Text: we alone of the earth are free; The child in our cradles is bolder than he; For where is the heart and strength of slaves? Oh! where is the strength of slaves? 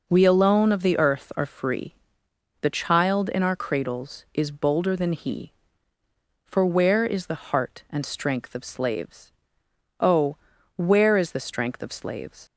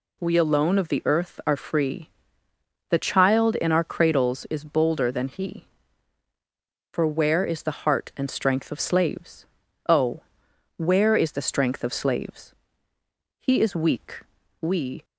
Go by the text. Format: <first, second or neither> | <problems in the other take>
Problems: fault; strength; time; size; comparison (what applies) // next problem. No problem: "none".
first | goes on to say "He is weak we"; from 13.4 s on; 1.6 s long